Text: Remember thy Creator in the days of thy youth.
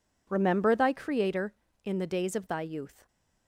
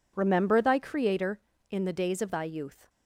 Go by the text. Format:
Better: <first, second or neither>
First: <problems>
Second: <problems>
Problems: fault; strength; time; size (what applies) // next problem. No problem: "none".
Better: neither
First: none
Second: none